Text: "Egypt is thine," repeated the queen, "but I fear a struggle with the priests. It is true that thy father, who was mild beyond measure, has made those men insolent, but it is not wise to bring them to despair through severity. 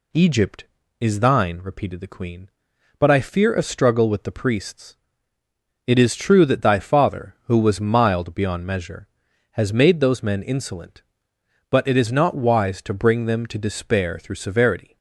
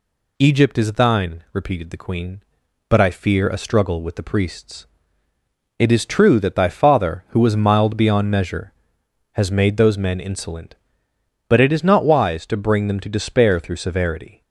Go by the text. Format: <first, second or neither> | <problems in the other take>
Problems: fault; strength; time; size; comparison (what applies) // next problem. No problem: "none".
neither | none